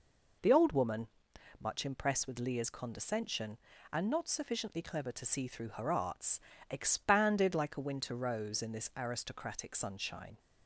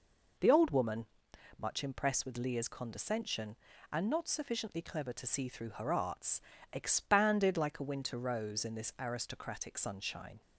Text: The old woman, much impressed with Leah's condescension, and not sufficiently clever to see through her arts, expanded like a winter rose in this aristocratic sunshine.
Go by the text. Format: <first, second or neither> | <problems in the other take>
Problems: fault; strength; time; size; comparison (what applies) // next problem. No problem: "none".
neither | none